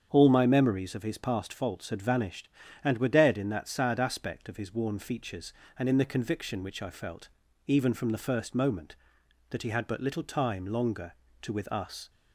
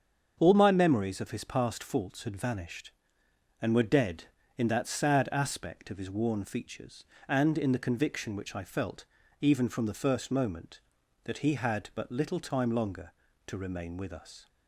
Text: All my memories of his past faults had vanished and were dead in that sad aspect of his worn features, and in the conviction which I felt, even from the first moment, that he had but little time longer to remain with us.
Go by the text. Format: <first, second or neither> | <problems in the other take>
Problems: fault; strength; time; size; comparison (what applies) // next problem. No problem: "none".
second | starts louder than the rest; strong; until 1.1 s; 7.5 dB; strong in the second // skips "remain"; at 11.5 s